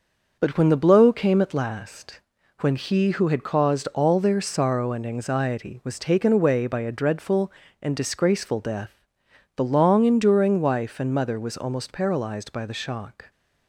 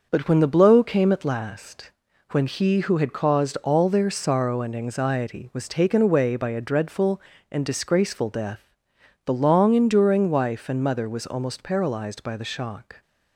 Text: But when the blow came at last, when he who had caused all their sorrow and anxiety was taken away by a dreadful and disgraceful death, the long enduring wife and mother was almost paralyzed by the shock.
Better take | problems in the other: neither | none

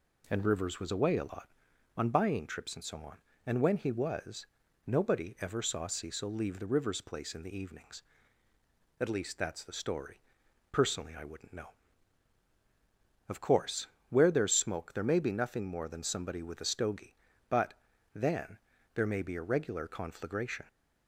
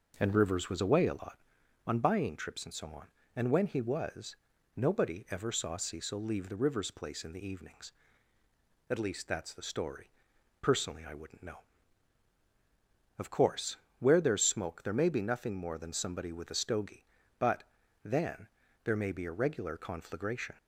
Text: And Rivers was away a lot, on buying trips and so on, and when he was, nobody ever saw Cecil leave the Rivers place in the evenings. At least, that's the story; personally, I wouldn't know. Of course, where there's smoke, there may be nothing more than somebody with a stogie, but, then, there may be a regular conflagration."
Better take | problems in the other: first | starts louder than the rest; noticeable; until 1.2 s; 5.5 dB

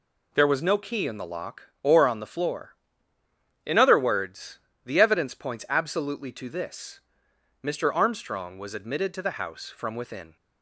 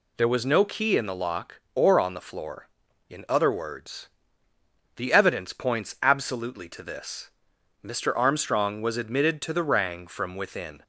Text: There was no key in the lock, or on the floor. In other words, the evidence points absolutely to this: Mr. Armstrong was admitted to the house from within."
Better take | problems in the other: first | says "rang" for "house"; at 9.6 s

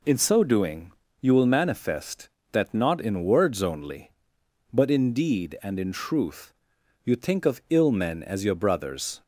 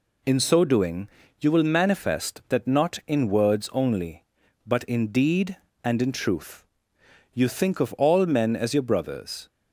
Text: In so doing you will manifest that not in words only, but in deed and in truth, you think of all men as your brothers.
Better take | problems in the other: second | pauses between "doing" and "you"; slight; at 0.8 s; 0.30 s long; slight in the second // says "ill" for "all"; at 7.6 s

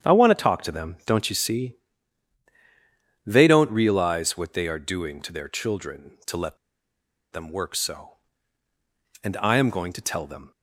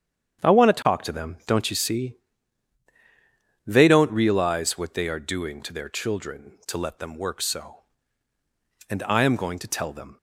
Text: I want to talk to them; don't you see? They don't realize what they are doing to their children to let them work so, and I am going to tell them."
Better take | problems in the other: second | starts louder than the rest; strong; until 1.1 s; 8.5 dB; strong in the second // pauses between "let" and "them"; noticeable; at 6.5 s; 0.75 s long

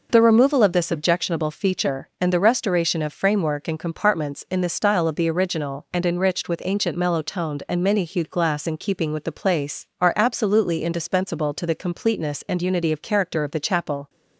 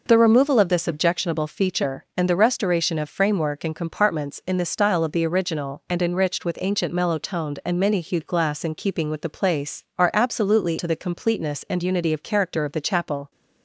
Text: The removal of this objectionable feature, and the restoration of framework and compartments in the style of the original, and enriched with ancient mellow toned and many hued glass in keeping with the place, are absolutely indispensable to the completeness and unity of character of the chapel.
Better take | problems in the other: first | skips "indispensable"; at 10.7 s

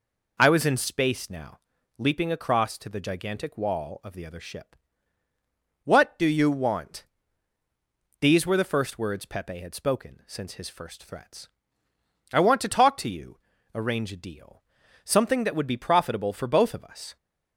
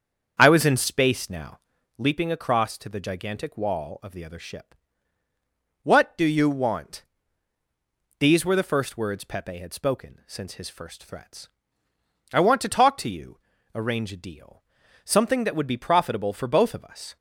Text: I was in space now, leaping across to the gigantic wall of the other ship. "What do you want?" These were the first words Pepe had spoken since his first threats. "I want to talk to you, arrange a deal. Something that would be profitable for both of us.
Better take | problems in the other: first | starts louder than the rest; strong; until 1.9 s; 7 dB

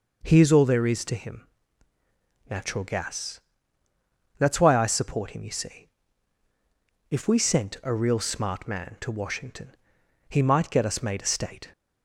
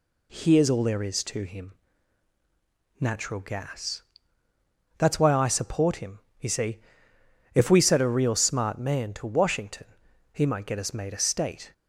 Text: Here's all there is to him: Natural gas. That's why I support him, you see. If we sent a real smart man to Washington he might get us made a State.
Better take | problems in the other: first | says "set" for "sent"; at 7.8 s // pauses between "Washington" and "he"; at 9.8 s; 0.44 s long; noticeable in the first

